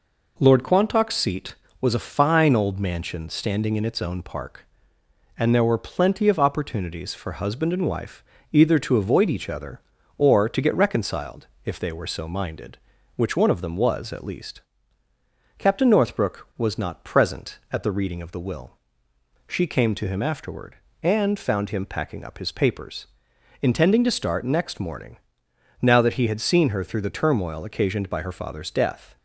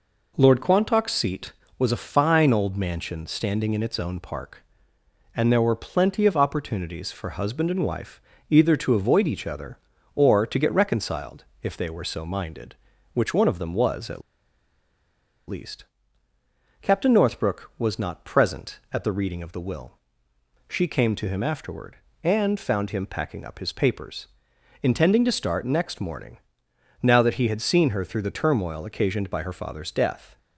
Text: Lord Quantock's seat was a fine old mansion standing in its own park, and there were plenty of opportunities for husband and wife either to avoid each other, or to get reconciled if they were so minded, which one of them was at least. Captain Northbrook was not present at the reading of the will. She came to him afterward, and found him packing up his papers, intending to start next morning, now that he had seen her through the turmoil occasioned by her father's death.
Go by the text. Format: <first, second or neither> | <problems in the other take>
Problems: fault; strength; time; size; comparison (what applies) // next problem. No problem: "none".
first | pauses between "wife" and "either"; slight; at 8.1 s; 0.30 s long; slight in the first // pauses between "reconciled" and "if"; slight; at 11.4 s; 0.18 s long; slight in the first // pauses between "at" and "least"; strong; at 14.2 s; 1.2 s long